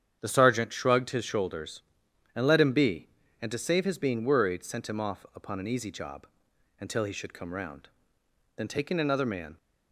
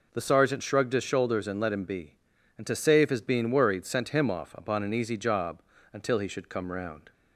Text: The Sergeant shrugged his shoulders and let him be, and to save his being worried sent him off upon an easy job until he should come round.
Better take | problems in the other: second | starts louder than the rest; strong; until 1.2 s; 8.5 dB // pauses between "job" and "until"; noticeable; at 6.2 s; 0.52 s long; slight in the second // goes on to say "Then taking another man"; noticeable; from 8.5 s on; 1.0 s long

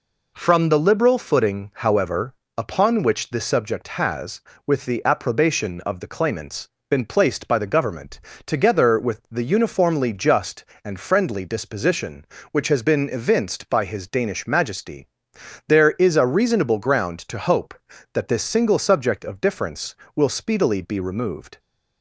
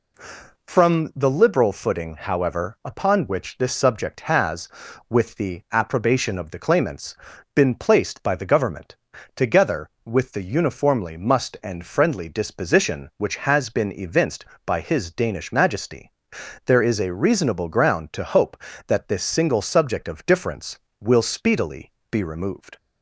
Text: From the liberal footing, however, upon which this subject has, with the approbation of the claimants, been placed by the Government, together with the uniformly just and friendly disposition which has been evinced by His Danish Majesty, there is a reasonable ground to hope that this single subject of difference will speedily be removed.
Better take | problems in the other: first | says "must" for "just"; at 11.1 s // pauses between "speedily" and "be"; slight; at 21.9 s; 0.18 s long

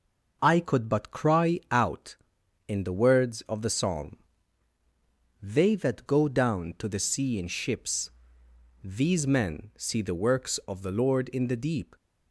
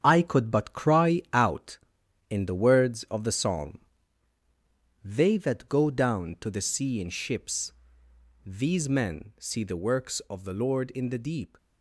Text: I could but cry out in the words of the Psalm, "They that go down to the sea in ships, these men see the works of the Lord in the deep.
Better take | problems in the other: first | gets quieter; strong; throughout; 9.5 dB

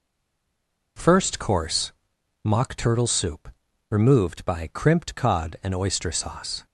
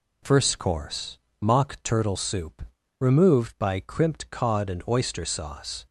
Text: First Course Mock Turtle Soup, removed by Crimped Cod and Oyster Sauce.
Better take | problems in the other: second | stays silent before the first word; slight; until 0.9 s; 0.9 s long // pauses between "Course" and "Mock"; noticeable; at 1.9 s; 0.50 s long; slight in the second

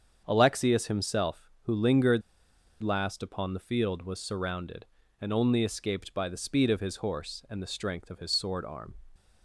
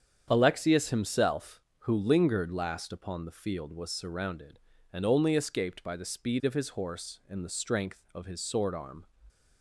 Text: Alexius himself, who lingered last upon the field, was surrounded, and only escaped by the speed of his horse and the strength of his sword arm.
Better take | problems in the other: second | starts louder than the rest; strong; until 1.2 s; 7.5 dB; strong in the second // pauses between "lingered" and "last"; noticeable; at 2.2 s; 0.60 s long

